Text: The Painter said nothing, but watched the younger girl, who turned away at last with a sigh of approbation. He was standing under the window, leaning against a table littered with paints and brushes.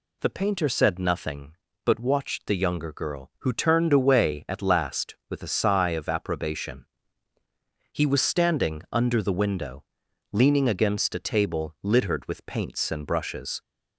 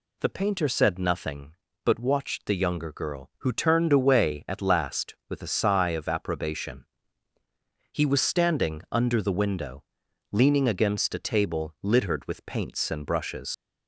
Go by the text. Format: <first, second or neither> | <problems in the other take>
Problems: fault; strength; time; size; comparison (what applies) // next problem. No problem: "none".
first | leaves "brushes" unfinished; at 13.5 s; 55 ms